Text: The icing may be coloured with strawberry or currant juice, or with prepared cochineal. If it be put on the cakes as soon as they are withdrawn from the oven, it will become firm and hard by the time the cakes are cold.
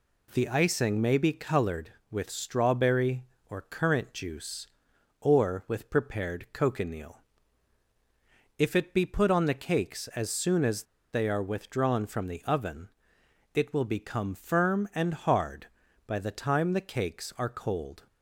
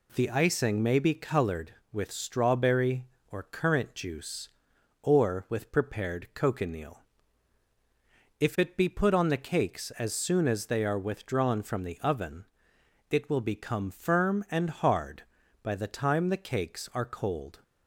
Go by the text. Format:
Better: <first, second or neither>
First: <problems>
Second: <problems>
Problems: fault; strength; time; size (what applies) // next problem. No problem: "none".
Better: second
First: pauses between "as" and "they"; slight; at 10.8 s; 0.29 s long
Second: none